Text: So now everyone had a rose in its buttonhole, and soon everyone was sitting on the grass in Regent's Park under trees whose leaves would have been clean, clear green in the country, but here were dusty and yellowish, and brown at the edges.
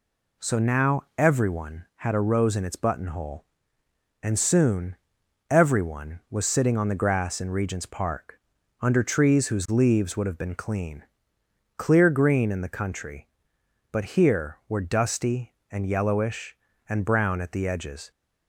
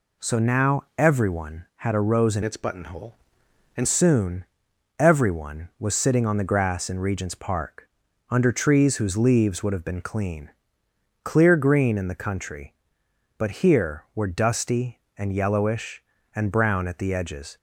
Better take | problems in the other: first | changes voice from "its" to "and"; from 2.4 to 3.8 s; 1.4 s long // pauses between "soon" and "everyone"; noticeable; at 4.4 s; 0.56 s long; noticeable in the first // pauses between "Park" and "under"; at 7.8 s; 0.42 s long; also in the first

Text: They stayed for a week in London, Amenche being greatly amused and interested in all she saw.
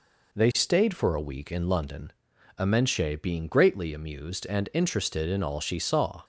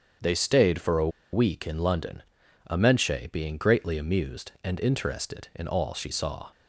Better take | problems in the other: first | starts louder than the rest; strong; until 1.4 s; 7.5 dB // pauses between "a" and "week"; slight; at 1.0 s; 0.23 s long

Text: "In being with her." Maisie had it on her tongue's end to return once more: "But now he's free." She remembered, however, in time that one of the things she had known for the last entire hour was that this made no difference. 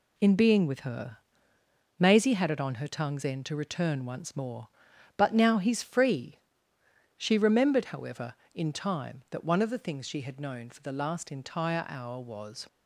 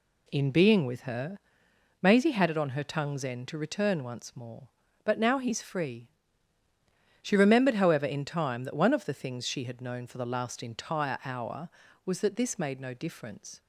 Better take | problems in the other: second | stops before "that this made no difference"; at 12.6 s

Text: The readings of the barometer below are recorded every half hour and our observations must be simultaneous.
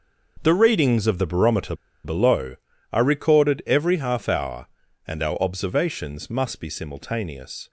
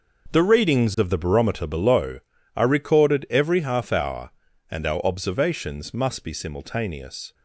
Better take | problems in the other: second | starts louder than the rest; until 1.4 s; 6 dB; also in the second // pauses between "barometer" and "below"; slight; at 1.7 s; 0.30 s long

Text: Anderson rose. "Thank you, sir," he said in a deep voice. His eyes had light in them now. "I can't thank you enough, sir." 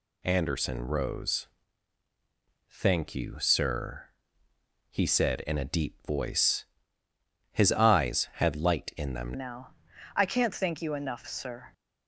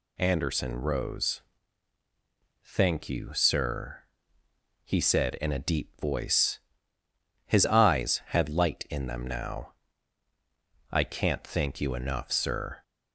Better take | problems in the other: second | changes voice at "now"; from 9.3 s on; 2.4 s long

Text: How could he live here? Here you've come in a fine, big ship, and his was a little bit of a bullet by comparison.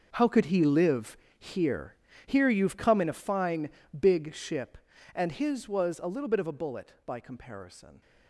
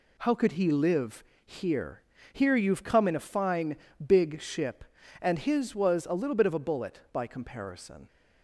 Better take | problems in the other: second | gets quieter; strong; throughout; 14 dB // pauses between "live" and "here"; slight; at 1.1 s; 0.22 s long; slight in the second

